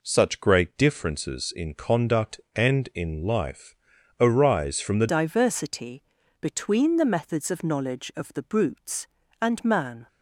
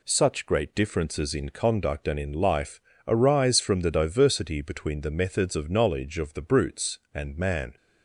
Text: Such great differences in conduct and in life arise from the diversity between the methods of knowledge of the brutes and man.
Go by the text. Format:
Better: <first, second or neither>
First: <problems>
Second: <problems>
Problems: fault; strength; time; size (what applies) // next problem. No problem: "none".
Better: second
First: pauses between "life" and "arise"; at 3.7 s; 0.44 s long // changes voice at "diversity"; from 5.0 s on; 5.0 s long // pauses between "diversity" and "between"; at 6.0 s; 0.38 s long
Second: pauses between "life" and "arise"; slight; at 2.8 s; 0.26 s long